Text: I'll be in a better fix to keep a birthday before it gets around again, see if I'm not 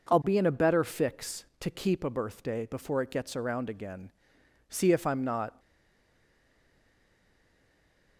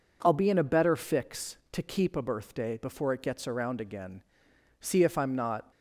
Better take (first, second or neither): second